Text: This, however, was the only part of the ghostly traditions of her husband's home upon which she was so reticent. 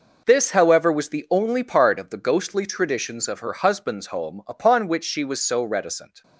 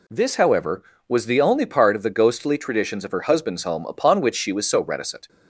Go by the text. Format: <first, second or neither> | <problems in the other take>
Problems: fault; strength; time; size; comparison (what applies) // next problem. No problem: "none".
neither | none